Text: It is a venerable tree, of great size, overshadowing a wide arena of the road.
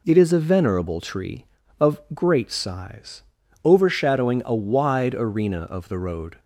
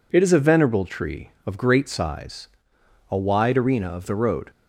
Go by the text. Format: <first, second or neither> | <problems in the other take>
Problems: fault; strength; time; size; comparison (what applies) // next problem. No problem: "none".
first | skips "overshadowing"; at 2.7 s